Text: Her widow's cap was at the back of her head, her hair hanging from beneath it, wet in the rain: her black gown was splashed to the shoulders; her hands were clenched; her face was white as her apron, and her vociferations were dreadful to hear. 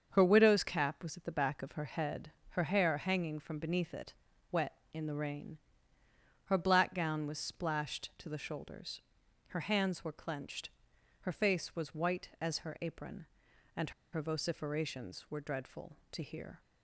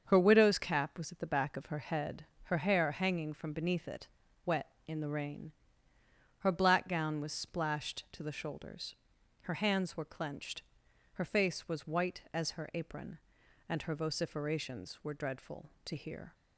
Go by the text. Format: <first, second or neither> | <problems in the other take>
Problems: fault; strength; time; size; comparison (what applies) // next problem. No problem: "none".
second | starts louder than the rest; until 1.1 s; 7 dB; also in the second // pauses between "and" and "her"; slight; at 13.9 s; 0.21 s long